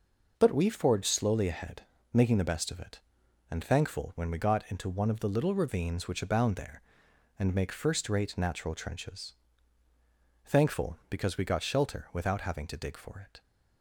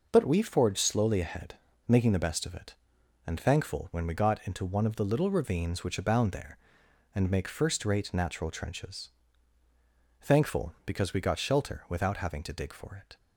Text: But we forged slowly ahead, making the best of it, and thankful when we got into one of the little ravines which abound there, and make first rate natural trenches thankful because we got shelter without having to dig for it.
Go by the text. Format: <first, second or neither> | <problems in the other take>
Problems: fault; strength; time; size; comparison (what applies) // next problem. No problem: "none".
neither | pauses between "trenches" and "thankful"; the same in both